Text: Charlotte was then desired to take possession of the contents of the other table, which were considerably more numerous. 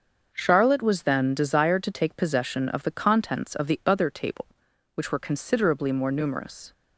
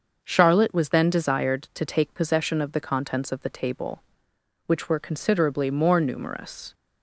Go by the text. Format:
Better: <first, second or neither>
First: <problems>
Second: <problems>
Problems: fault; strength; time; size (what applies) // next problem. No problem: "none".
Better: first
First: starts louder than the rest; until 1.3 s; 6.5 dB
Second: starts louder than the rest; until 1.2 s; 6.5 dB // skips "other"; at 3.4 s